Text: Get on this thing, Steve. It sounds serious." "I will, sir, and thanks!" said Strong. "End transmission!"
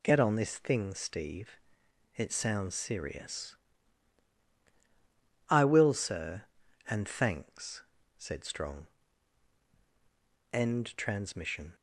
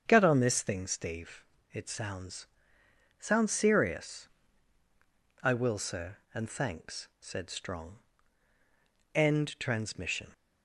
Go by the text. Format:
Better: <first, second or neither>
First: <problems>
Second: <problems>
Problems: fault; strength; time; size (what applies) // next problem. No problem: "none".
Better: first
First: none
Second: starts louder than the rest; strong; until 1.0 s; 7.5 dB // says "sounds" twice; at 3.1 s